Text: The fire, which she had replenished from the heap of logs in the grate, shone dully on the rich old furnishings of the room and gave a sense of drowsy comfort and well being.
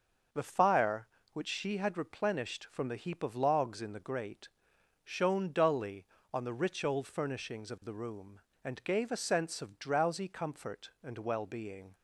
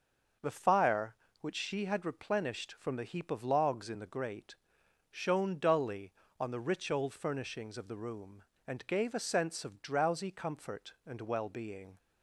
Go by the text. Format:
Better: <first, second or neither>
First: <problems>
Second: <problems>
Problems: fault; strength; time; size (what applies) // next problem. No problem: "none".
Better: neither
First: starts louder than the rest; until 1.5 s; 6 dB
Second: starts louder than the rest; until 1.6 s; 6 dB